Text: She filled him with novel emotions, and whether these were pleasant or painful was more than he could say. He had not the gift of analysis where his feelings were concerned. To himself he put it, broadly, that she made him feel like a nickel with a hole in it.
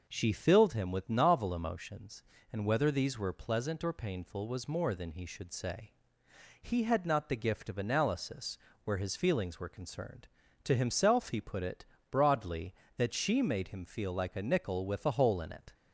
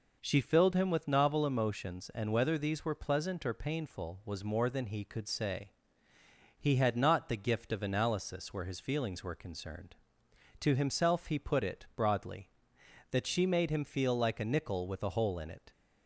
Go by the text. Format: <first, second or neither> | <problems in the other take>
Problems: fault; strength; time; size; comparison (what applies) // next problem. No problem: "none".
second | says "should" for "could"; at 5.2 s // pauses between "analysis" and "where"; slight; at 8.5 s; 0.26 s long